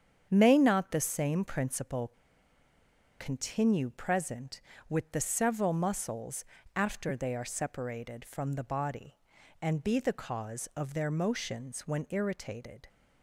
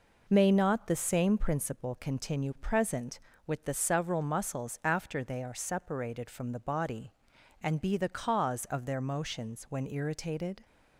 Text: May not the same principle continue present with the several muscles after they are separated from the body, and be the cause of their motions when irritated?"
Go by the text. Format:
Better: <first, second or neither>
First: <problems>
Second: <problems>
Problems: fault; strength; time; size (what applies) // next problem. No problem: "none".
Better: second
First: starts louder than the rest; strong; until 1.3 s; 7.5 dB // pauses between "principle" and "continue"; at 2.1 s; 1.0 s long // pauses between "muscles" and "after"; slight; at 6.4 s; 0.32 s long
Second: none